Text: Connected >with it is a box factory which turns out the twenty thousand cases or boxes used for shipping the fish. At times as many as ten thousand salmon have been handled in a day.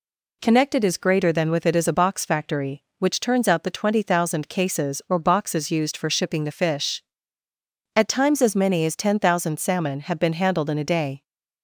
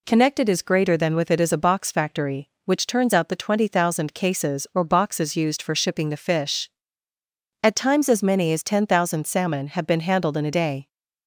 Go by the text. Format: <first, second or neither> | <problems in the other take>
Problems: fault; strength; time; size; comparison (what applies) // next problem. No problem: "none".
neither | none